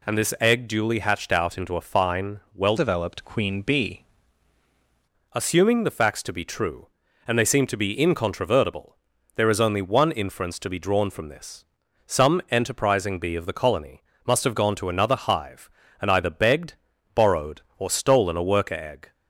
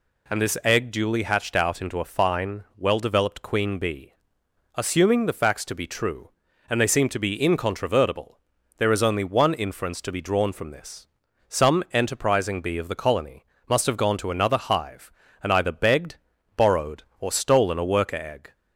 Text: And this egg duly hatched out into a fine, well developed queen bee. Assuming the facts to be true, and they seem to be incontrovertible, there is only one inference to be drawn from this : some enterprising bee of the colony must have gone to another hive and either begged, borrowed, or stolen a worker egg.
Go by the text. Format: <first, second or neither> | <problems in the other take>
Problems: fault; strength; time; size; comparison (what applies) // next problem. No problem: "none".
second | changes voice from "developed" to "bee"; from 2.7 to 4.0 s; 1.3 s long // pauses between "colony" and "must"; slight; at 14.0 s; 0.24 s long; slight in the second